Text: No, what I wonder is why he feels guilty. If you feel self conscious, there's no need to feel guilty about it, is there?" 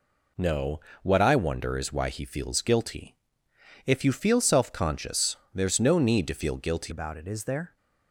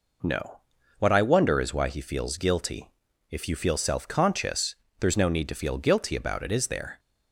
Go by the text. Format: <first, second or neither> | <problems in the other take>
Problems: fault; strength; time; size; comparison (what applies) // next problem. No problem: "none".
second | changes voice at "about"; from 6.8 s on; 0.9 s long